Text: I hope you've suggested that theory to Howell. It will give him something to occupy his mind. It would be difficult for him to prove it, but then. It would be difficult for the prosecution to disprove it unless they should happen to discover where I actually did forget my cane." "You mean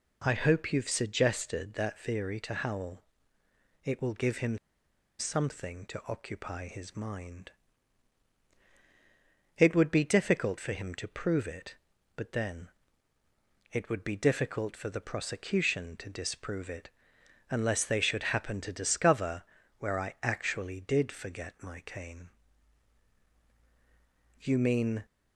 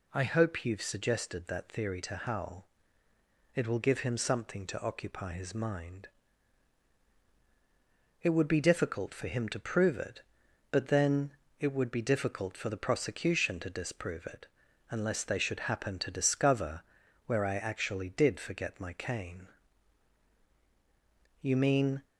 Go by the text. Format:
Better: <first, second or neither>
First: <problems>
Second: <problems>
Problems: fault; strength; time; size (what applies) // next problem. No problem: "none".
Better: second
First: pauses between "him" and "something"; noticeable; at 4.5 s; 0.62 s long // pauses between "it" and "unless"; noticeable; at 16.8 s; 0.60 s long // pauses between "discover" and "where"; slight; at 19.4 s; 0.36 s long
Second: pauses between "it" and "unless"; noticeable; at 14.4 s; 0.46 s long // pauses between "discover" and "where"; at 16.8 s; 0.42 s long